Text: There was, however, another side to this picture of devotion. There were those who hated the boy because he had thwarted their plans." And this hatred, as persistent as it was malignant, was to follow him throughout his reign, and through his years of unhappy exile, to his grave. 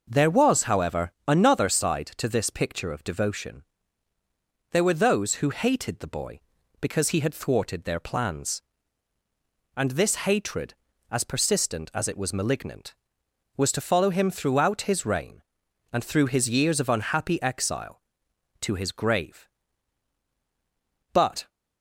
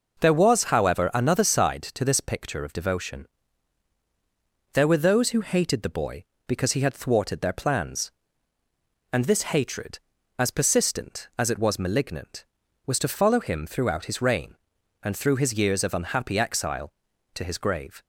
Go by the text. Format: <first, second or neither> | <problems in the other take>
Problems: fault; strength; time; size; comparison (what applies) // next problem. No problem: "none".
second | goes on to say "But"; slight; from 21.1 s on; 0.36 s long